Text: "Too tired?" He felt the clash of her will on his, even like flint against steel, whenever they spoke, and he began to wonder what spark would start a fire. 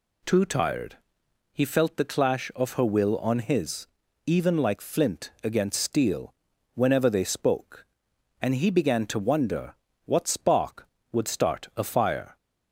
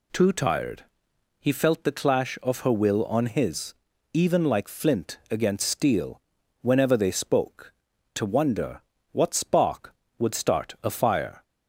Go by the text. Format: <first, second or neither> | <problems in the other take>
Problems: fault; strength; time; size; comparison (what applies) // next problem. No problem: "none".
first | skips "and he began"; at 7.9 s // pauses between "wonder" and "what"; slight; at 8.8 s; 0.32 s long; slight in the first